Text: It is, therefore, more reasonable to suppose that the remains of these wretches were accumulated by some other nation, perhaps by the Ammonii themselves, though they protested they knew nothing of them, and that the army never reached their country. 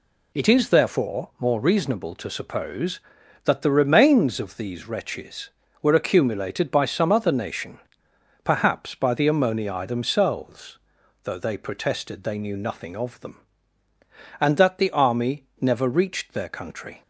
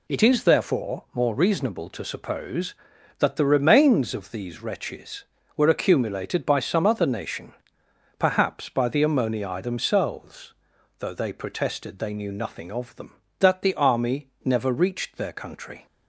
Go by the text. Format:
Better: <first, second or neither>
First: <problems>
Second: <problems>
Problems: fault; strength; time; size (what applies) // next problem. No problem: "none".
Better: first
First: pauses between "army" and "never"; slight; at 15.4 s; 0.16 s long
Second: skips "and"; at 13.2 s // pauses between "army" and "never"; slight; at 14.2 s; 0.16 s long